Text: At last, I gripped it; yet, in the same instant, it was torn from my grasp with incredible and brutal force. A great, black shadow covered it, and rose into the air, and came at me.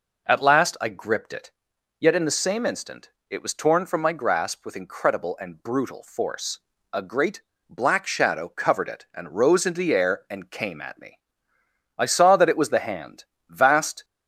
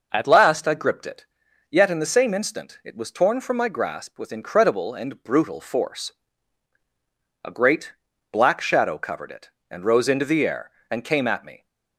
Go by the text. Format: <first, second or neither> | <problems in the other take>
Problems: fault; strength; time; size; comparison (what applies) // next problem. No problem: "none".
second | goes on to say "I saw that it was the Hand vast"; strong; from 11.9 s on; 2.0 s long